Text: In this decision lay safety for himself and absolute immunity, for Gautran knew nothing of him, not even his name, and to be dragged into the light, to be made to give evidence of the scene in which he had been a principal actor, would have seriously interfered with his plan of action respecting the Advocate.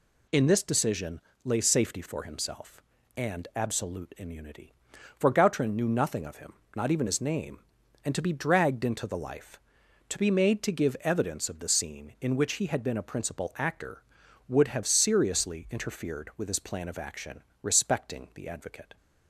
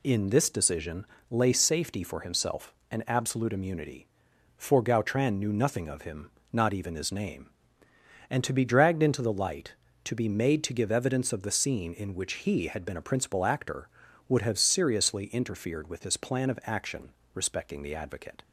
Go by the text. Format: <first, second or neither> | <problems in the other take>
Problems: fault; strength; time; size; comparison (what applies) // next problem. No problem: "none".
second | pauses between "decision" and "lay"; slight; at 1.2 s; 0.24 s long; slight in the second // says "life" for "light"; at 9.1 s // pauses between "action" and "respecting"; slight; at 17.4 s; 0.18 s long; slight in the second